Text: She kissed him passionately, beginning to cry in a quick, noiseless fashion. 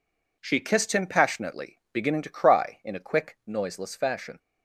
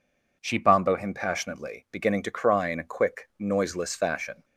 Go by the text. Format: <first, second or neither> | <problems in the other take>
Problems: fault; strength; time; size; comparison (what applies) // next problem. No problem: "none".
first | says "bombo" for "kissed"; at 0.5 s